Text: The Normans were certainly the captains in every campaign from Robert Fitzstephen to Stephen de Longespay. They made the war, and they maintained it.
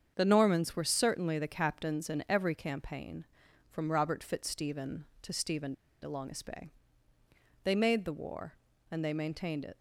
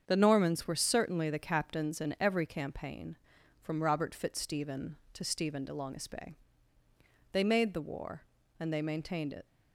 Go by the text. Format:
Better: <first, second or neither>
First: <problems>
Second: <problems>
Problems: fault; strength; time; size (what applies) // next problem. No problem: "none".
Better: second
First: starts louder than the rest; strong; until 1.1 s; 7.5 dB // pauses between "Stephen" and "de"; slight; at 5.7 s; 0.27 s long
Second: starts louder than the rest; strong; until 1.0 s; 7.5 dB